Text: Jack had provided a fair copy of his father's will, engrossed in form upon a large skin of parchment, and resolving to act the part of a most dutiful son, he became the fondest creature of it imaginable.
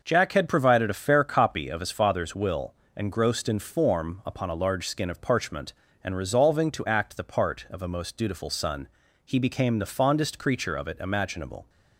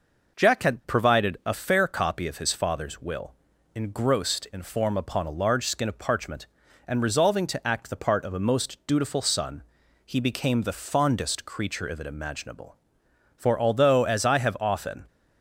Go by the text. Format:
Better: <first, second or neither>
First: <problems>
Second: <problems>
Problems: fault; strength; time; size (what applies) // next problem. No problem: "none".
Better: first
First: none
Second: goes on to say "For although as I have often"; strong; from 13.3 s on; 1.6 s long